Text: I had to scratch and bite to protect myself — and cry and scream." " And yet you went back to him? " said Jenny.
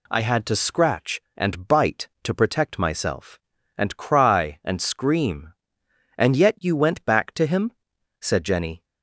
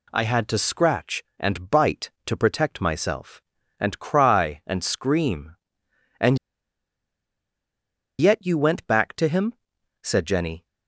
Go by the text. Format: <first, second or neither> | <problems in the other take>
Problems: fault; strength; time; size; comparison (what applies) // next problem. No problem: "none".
first | pauses between "And" and "yet"; strong; at 6.3 s; 1.8 s long